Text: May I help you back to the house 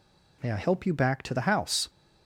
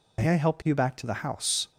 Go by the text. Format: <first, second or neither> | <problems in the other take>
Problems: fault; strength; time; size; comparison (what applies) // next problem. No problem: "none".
first | loses the start of "May"; at 0.1 s; 85 ms